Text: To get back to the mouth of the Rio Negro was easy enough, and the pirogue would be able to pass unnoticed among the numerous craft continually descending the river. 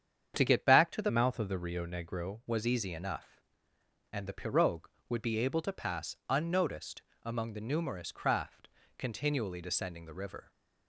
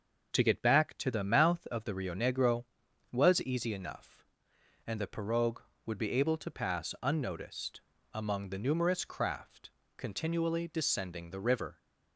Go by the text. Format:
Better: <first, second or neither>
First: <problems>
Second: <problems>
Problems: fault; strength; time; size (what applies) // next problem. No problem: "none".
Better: second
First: starts louder than the rest; strong; until 1.3 s; 8 dB // changes voice from "mouth" to "Negro"; from 1.0 to 2.3 s; 1.3 s long // pauses between "unnoticed" and "among"; slight; at 7.0 s; 0.22 s long // pauses between "craft" and "continually"; slight; at 8.6 s; 0.30 s long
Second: starts louder than the rest; until 1.3 s; 7 dB // pauses between "unnoticed" and "among"; slight; at 7.8 s; 0.30 s long // pauses between "craft" and "continually"; slight; at 9.6 s; 0.26 s long